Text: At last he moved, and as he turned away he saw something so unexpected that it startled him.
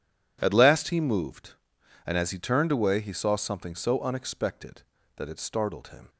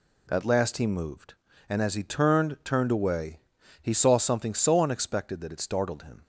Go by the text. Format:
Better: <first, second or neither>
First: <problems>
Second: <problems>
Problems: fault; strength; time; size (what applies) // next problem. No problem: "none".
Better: first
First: none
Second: says "turned" twice; at 2.6 s // pauses between "away" and "he"; at 3.4 s; 0.40 s long